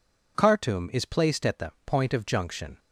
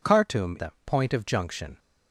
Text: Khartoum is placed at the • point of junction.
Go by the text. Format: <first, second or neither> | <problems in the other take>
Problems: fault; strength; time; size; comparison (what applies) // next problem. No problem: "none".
first | skips "is placed at"; at 0.5 s